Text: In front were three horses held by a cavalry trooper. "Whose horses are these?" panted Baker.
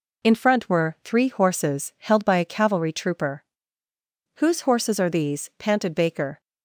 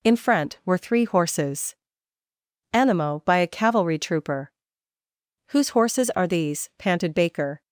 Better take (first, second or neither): first